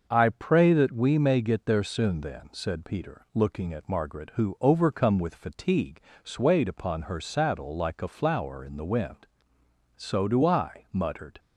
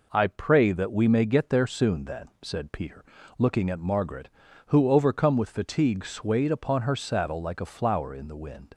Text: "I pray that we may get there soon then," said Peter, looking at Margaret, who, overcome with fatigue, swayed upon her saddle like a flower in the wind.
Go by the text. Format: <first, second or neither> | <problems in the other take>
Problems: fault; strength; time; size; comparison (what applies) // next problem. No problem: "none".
second | starts louder than the rest; noticeable; until 1.1 s; 6 dB // goes on to say "So do I muttered"; from 9.9 s on; 1.4 s long